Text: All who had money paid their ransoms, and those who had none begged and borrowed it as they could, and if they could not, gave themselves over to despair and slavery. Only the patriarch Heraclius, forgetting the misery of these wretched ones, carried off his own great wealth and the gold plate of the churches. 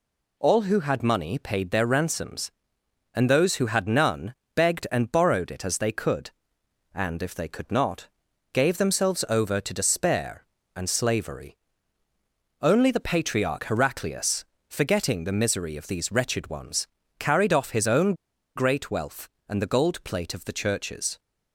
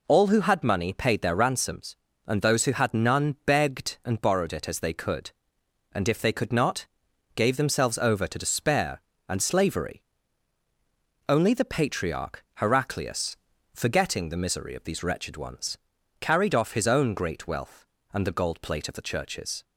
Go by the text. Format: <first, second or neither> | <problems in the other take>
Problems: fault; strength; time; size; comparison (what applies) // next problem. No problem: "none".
second | pauses between "none" and "begged"; slight; at 4.3 s; 0.22 s long // pauses between "own" and "great"; at 18.1 s; 0.42 s long